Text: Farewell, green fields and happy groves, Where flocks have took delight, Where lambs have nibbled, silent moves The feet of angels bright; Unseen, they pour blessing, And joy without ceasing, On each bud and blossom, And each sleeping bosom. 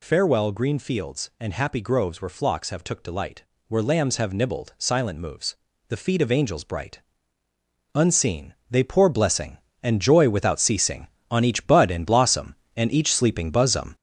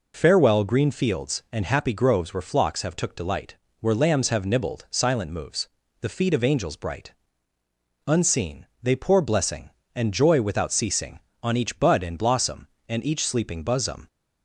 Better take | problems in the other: second | gets louder; noticeable; throughout; 5.5 dB // pauses between "moves" and "The"; slight; at 5.5 s; 0.32 s long; slight in the second

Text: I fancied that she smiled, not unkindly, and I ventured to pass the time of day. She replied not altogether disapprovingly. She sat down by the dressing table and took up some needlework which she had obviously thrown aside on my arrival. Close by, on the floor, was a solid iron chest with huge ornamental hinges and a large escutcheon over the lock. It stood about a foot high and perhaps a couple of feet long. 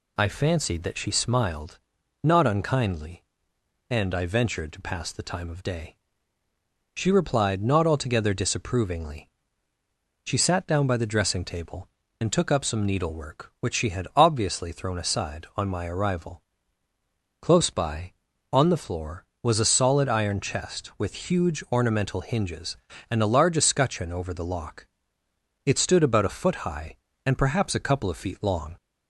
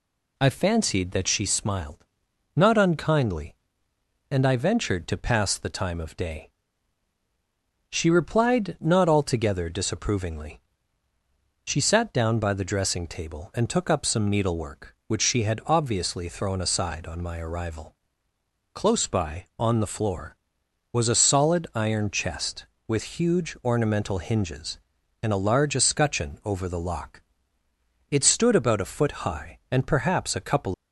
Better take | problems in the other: first | stops before "of feet long"; at 30.7 s

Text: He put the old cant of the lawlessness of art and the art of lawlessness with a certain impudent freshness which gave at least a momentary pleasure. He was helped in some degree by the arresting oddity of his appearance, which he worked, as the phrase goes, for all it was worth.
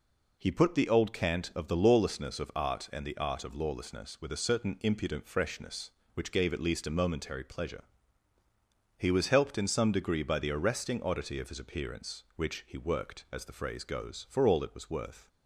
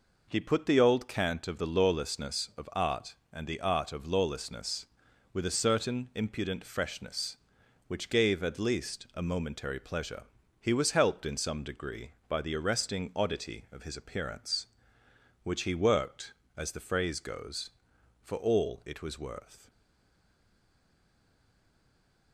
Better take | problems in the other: first | stays silent after the last word; strong; from 19.6 s on; 2.7 s long

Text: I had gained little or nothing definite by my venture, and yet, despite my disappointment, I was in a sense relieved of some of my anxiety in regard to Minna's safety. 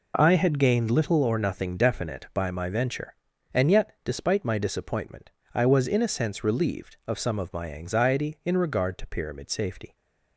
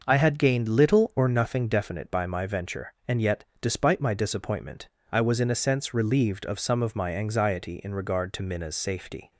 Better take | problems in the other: second | says "Pyramid" for "Minna's"; at 9.0 s

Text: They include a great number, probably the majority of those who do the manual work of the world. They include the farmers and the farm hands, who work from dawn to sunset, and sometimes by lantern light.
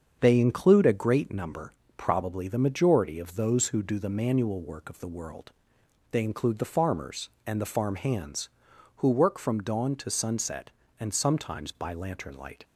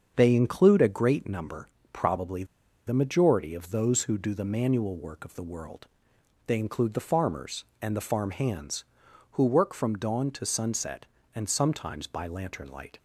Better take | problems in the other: first | starts louder than the rest; until 1.1 s; 7 dB; also in the first // pauses between "probably" and "the"; at 2.4 s; 0.42 s long

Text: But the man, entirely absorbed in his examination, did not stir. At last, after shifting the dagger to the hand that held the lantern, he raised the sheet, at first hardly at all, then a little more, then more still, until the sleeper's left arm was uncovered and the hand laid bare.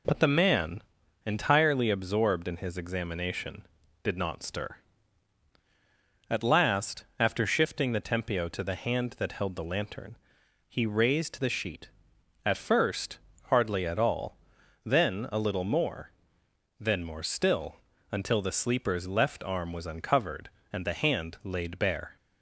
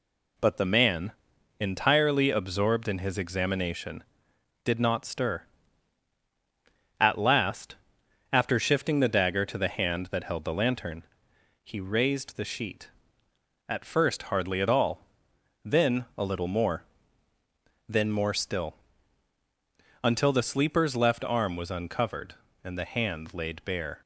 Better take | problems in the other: second | says "tempio" for "dagger"; at 7.9 s // pauses between "first" and "hardly"; slight; at 13.1 s; 0.32 s long

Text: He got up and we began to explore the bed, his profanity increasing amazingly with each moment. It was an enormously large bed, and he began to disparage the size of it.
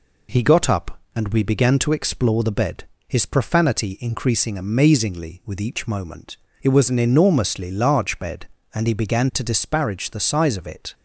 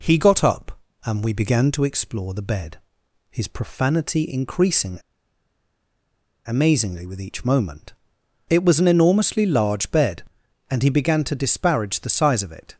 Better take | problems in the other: first | pauses between "increasing" and "amazingly"; strong; at 4.9 s; 1.4 s long

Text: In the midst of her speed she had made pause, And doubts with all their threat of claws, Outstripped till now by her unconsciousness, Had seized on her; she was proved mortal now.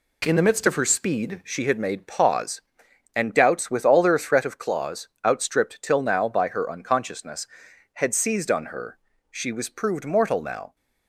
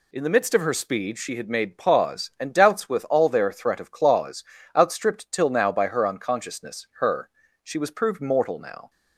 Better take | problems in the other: first | skips "Had seized on"; at 6.9 s

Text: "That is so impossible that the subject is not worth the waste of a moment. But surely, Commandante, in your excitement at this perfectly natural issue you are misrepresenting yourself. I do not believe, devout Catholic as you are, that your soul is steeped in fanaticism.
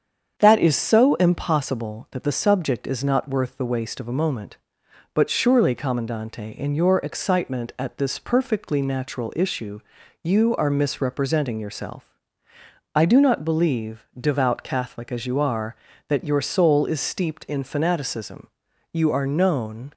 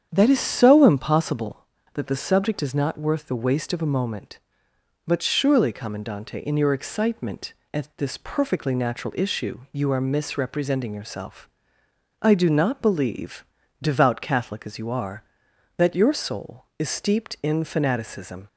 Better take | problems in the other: second | starts louder than the rest; strong; until 1.3 s; 7.5 dB; strong in the second // pauses between "issue" and "you"; at 9.7 s; 0.44 s long // goes on to say "You are known"; noticeable; from 18.9 s on; 1.0 s long

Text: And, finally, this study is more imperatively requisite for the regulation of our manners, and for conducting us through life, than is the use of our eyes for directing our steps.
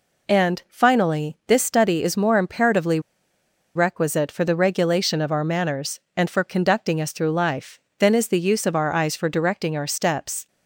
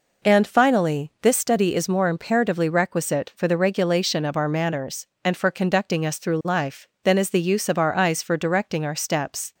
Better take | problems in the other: second | pauses between "imperatively" and "requisite"; noticeable; at 2.9 s; 0.75 s long

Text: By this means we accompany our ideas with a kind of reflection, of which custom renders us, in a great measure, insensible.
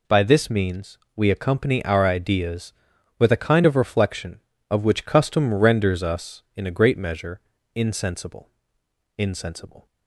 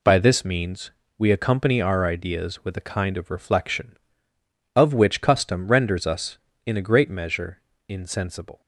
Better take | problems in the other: second | pauses between "means" and "we"; slight; at 0.9 s; 0.18 s long; slight in the second // says "insensible" twice; at 9.1 s

